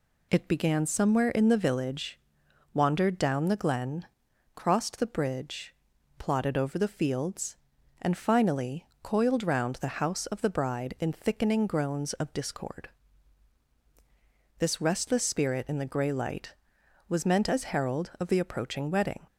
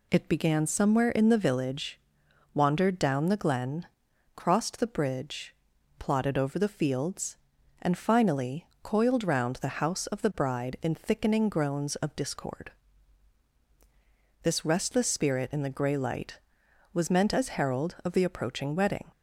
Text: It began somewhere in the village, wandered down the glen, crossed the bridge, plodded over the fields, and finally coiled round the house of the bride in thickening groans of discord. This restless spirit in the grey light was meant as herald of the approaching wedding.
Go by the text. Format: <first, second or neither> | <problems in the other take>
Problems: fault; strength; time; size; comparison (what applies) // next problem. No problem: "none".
neither | pauses between "finally" and "coiled"; slight; the same in both